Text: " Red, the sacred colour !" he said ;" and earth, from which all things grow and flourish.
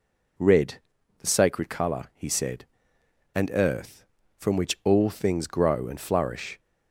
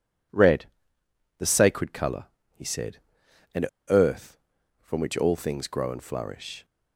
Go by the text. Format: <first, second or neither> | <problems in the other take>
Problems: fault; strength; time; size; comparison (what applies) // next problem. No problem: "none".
first | pauses between "and" and "earth"; slight; at 3.6 s; 0.24 s long